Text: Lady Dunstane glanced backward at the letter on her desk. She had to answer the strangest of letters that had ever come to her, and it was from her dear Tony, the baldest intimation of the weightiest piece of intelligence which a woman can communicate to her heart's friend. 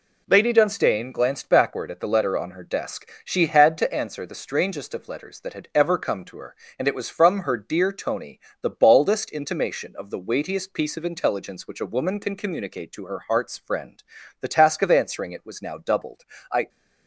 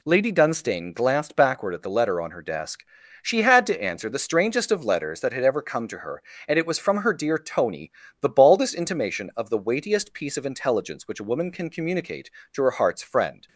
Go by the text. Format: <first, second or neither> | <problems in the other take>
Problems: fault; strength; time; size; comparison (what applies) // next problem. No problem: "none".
second | goes on to say "The task of answering it was now doubled I"; strong; from 14.4 s on; 2.2 s long